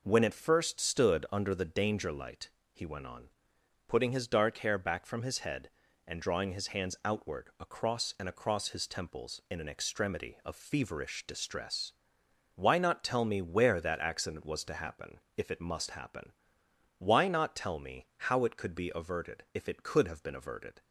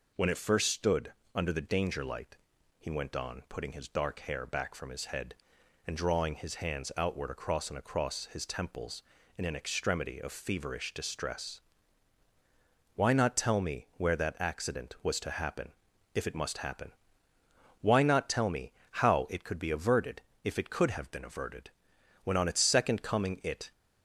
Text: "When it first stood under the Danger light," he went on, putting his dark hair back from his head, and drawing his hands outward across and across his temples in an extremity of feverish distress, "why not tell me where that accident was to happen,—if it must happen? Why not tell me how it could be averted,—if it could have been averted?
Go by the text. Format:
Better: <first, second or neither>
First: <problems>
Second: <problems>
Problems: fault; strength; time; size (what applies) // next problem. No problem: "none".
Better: first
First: pauses between "me" and "how"; slight; at 18.0 s; 0.22 s long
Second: pauses between "stood" and "under"; slight; at 1.1 s; 0.20 s long // pauses between "me" and "how"; slight; at 18.7 s; 0.20 s long // goes on to say "When on its second coming it"; from 22.2 s on; 1.4 s long